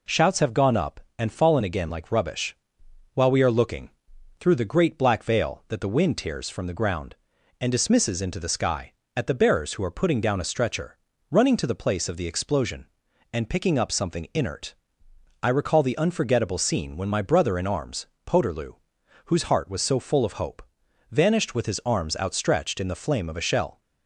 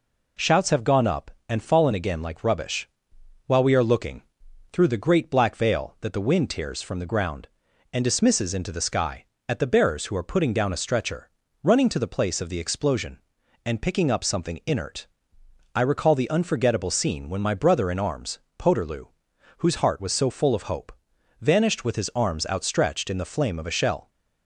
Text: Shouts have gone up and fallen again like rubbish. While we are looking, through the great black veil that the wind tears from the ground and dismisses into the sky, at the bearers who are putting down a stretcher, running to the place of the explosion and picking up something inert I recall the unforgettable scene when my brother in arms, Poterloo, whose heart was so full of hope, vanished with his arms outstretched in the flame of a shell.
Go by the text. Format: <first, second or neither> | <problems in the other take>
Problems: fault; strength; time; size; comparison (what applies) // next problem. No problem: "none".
neither | pauses between "inert" and "I"; noticeable; the same in both